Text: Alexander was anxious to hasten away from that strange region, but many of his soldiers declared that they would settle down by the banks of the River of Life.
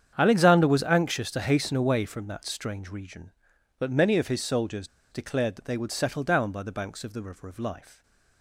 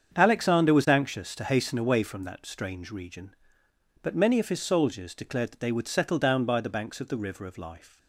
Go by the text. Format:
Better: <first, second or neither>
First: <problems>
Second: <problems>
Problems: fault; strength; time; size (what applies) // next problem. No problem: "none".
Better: second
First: starts louder than the rest; strong; until 1.1 s; 8.5 dB // pauses between "soldiers" and "declared"; slight; at 4.8 s; 0.24 s long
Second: starts louder than the rest; strong; until 1.1 s; 7.5 dB